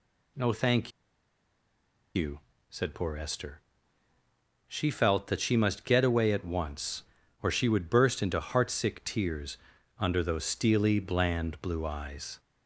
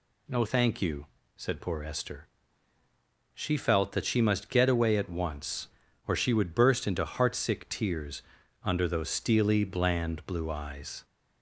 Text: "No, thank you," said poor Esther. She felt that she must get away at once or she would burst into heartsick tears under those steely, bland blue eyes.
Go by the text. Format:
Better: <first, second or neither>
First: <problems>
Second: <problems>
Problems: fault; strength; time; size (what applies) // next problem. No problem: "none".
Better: second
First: pauses between "thank" and "you"; strong; at 0.9 s; 1.2 s long // pauses between "tears" and "under"; at 9.5 s; 0.42 s long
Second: pauses between "tears" and "under"; at 8.2 s; 0.42 s long